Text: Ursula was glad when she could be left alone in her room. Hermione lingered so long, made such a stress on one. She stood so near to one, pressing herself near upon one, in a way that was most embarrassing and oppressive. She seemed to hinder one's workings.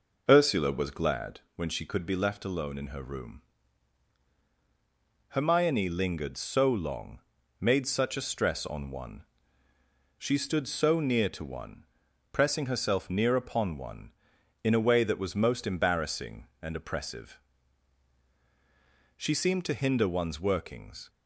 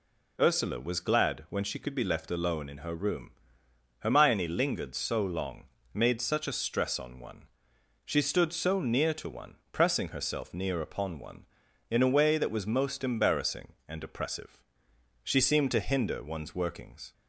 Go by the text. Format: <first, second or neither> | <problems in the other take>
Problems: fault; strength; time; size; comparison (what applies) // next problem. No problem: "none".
second | starts louder than the rest; noticeable; until 1.4 s; 5 dB // pauses between "glad" and "when"; slight; at 1.4 s; 0.16 s long